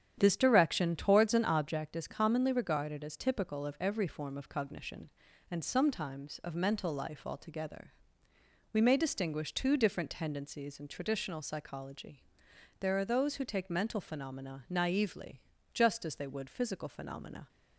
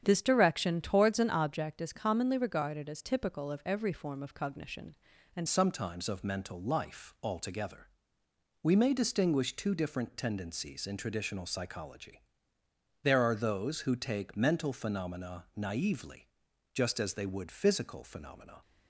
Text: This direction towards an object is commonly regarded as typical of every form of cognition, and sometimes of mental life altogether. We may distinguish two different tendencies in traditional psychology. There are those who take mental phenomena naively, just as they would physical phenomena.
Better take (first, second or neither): first